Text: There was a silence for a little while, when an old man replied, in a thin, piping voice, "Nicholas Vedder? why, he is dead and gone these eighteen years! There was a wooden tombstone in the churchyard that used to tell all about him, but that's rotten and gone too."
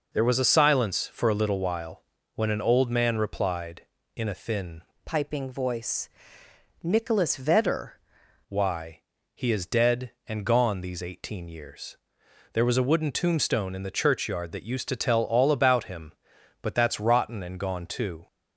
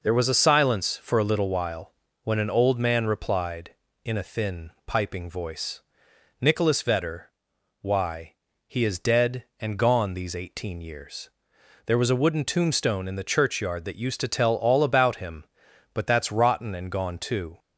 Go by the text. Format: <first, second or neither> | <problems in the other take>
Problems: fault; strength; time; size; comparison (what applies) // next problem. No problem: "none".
second | changes voice from "piping" to "Vedder"; from 5.0 to 7.9 s; 2.9 s long